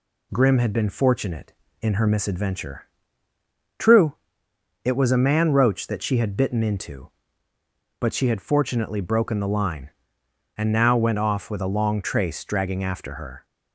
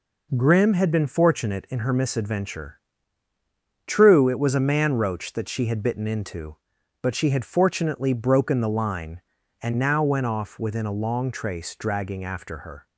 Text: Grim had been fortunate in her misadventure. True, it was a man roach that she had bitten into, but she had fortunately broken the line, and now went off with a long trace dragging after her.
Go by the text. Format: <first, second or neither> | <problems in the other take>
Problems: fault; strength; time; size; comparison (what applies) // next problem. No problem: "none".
first | says "within" for "with"; at 10.5 s